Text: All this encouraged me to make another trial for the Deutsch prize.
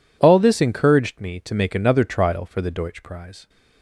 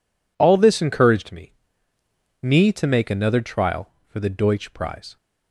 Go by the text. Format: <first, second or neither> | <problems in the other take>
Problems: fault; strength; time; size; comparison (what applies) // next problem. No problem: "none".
first | says "me" twice; at 2.4 s